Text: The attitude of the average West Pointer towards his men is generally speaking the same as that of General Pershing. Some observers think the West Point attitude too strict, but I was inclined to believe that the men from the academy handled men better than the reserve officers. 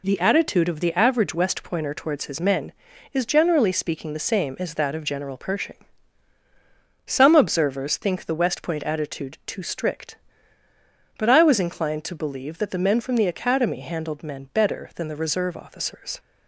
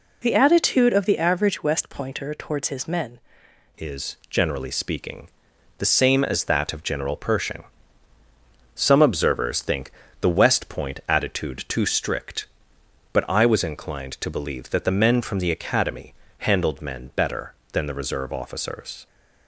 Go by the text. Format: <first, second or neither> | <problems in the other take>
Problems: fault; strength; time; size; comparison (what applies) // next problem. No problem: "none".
first | changes voice at "is"; from 3.7 s on; 15.3 s long // pauses between "speaking" and "the"; noticeable; at 5.2 s; 0.52 s long // pauses between "think" and "the"; slight; at 9.9 s; 0.32 s long // pauses between "academy" and "handled"; slight; at 16.1 s; 0.24 s long